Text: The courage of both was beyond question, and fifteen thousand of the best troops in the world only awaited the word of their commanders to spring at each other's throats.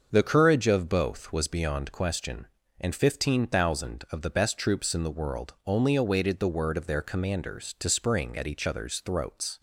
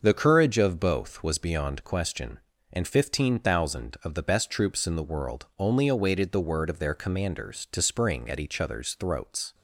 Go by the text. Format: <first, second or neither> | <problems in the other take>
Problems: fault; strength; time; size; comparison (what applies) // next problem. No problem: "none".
neither | starts louder than the rest; the same in both